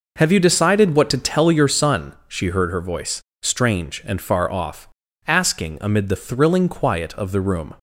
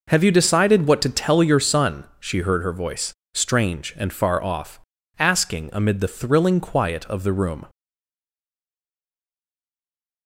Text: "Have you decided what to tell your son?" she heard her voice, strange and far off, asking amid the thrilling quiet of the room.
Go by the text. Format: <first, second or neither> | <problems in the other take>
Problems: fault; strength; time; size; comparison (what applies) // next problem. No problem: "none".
first | stays silent after the last word; strong; from 7.6 s on; 2.6 s long